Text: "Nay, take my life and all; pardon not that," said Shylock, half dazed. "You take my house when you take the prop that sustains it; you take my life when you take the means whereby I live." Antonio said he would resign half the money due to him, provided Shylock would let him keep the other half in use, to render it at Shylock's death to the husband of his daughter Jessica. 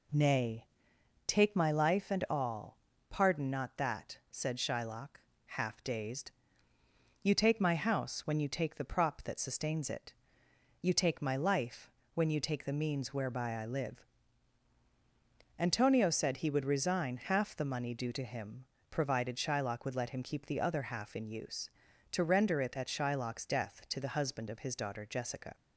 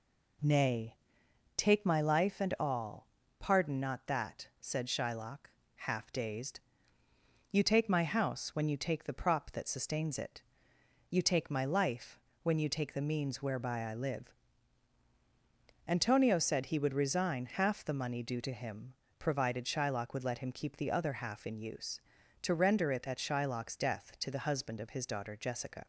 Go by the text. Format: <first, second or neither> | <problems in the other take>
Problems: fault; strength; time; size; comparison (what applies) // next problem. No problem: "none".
neither | pauses between "life" and "when"; slight; the same in both